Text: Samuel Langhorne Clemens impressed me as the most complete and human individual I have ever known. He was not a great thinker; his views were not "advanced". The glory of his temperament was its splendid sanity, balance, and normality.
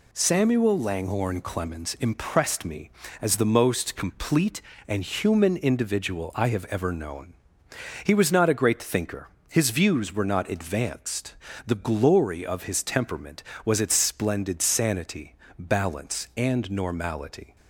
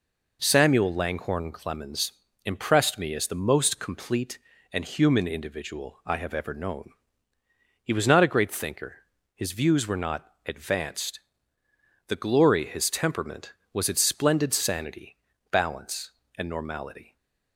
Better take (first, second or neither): first